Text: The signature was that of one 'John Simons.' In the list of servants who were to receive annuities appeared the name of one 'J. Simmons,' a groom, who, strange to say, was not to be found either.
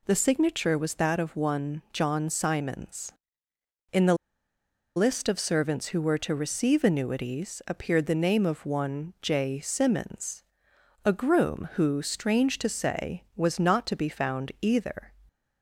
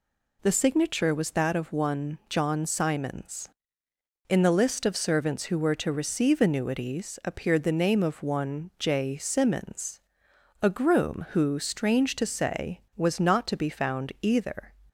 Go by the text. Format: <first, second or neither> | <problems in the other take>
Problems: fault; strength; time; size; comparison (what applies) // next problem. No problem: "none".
second | pauses between "the" and "list"; noticeable; at 4.1 s; 0.81 s long